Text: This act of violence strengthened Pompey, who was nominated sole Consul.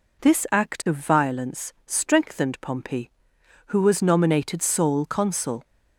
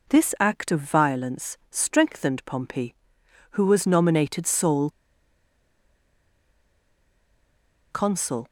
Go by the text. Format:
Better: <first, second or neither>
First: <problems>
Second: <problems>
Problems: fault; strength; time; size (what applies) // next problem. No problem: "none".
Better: first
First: none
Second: pauses between "sole" and "Consul"; strong; at 4.8 s; 3.0 s long